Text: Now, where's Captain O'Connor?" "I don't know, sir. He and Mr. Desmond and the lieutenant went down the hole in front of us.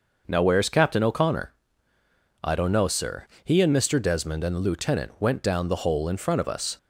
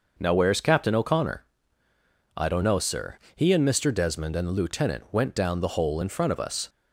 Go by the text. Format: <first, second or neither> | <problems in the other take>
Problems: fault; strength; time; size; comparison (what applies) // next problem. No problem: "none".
neither | none